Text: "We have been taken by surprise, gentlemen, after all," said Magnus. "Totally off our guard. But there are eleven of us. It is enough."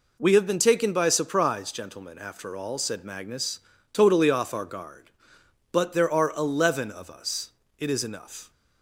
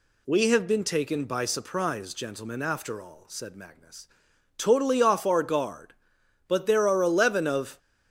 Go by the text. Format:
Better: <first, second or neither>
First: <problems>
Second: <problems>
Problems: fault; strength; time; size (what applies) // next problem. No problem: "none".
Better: first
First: none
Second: stops before "us It is enough"; at 7.7 s